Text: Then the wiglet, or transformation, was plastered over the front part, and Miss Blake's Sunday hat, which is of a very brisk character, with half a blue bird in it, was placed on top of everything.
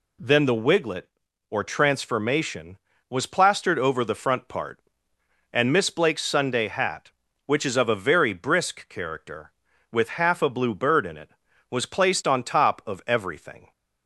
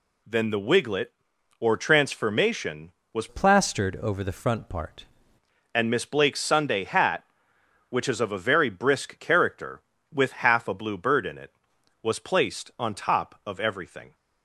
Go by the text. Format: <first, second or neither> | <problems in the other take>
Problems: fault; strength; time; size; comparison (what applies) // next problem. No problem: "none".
first | changes voice from "plastered" to "part"; from 3.2 to 5.0 s; 1.8 s long